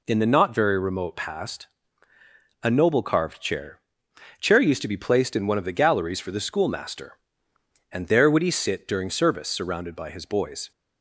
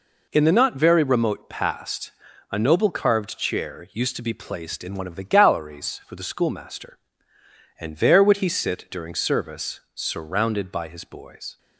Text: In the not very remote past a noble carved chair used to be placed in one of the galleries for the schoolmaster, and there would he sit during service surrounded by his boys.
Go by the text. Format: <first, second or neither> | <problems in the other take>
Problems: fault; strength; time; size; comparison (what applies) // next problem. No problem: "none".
second | pauses between "past" and "a"; noticeable; at 1.6 s; 0.94 s long; also in the second // says "chair" twice; at 4.4 s